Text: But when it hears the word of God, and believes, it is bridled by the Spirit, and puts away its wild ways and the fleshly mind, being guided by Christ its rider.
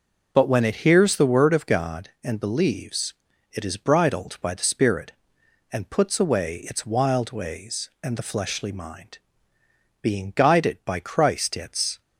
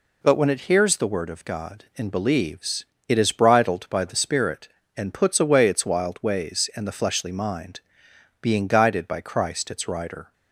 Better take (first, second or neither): second